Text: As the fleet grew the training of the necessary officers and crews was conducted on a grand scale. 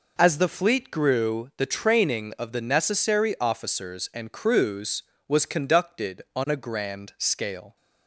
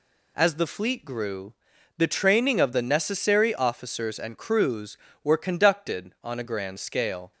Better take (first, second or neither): first